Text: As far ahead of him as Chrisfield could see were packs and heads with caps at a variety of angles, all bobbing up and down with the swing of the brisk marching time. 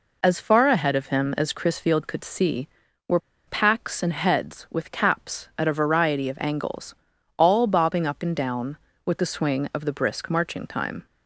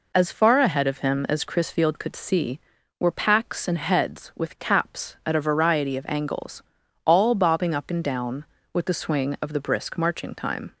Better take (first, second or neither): second